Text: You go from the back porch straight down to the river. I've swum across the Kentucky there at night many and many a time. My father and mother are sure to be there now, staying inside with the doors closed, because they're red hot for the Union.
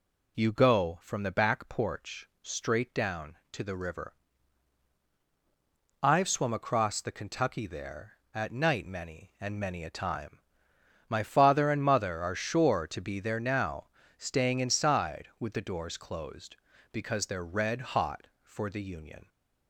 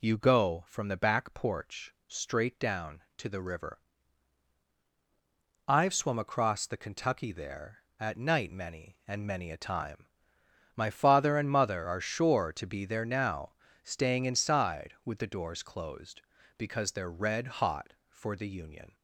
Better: neither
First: pauses between "porch" and "straight"; slight; at 2.2 s; 0.16 s long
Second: pauses between "porch" and "straight"; slight; at 1.9 s; 0.16 s long

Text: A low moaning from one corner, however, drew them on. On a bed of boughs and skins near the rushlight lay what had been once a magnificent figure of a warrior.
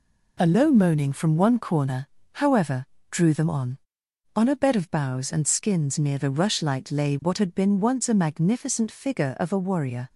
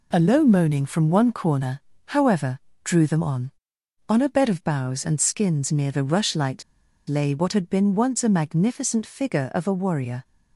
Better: first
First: none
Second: pauses between "rushlight" and "lay"; noticeable; at 6.6 s; 0.46 s long

